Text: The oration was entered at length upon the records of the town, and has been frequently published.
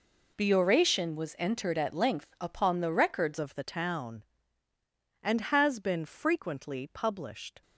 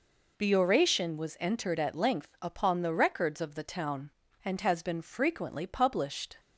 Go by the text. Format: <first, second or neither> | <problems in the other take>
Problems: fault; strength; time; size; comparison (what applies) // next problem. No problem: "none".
second | changes voice at "of"; from 3.3 s on; 4.3 s long